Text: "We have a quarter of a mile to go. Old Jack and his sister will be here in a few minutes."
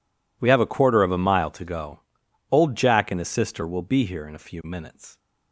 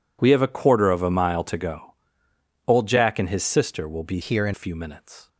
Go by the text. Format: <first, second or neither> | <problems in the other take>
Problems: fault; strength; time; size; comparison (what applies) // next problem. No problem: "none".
first | changes voice from "here" to "in"; from 4.2 to 4.5 s; 0.3 s long